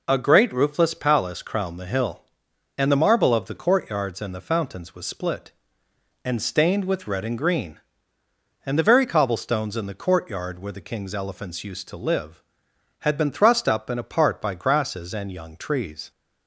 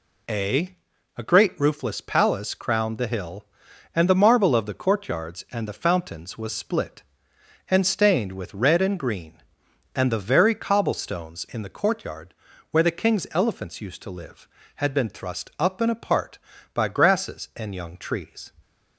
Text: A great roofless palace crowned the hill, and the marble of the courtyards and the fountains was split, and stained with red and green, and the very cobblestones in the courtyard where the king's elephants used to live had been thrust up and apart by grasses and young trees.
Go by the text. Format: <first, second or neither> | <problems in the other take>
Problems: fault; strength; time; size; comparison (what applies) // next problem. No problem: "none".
first | says "A" twice; at 1.1 s // pauses between "courtyard" and "where"; at 12.3 s; 0.38 s long